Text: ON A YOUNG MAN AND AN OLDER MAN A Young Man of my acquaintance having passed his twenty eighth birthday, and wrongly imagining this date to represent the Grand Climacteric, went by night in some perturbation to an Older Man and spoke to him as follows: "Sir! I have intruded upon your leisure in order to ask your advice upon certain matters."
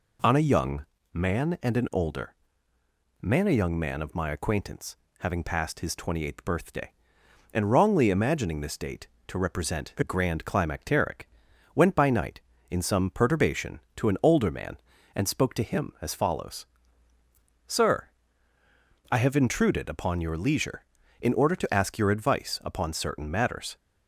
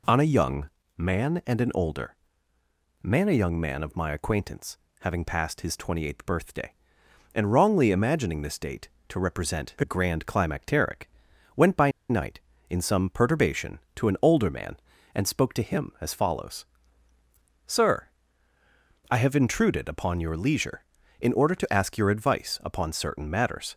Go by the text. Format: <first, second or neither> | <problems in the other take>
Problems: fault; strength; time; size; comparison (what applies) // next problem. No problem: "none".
first | pauses between "YOUNG" and "MAN"; slight; at 0.6 s; 0.30 s long; slight in the first // pauses between "OLDER" and "MAN"; noticeable; at 2.1 s; 0.88 s long; noticeable in the first // pauses between "acquaintance" and "having"; slight; at 4.7 s; 0.24 s long; slight in the first // pauses between "by" and "night"; slight; at 11.9 s; 0.19 s long